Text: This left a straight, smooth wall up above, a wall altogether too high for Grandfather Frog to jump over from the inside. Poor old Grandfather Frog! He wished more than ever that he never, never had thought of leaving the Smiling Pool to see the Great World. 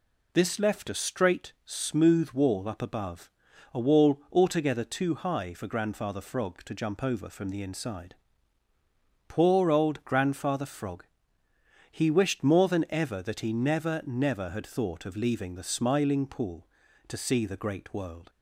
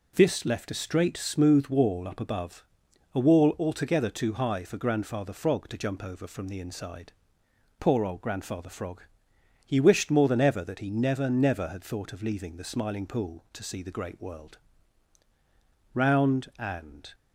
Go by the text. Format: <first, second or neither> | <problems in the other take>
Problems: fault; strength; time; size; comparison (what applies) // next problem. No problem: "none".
first | goes on to say "Round and"; noticeable; from 15.9 s on; 1.2 s long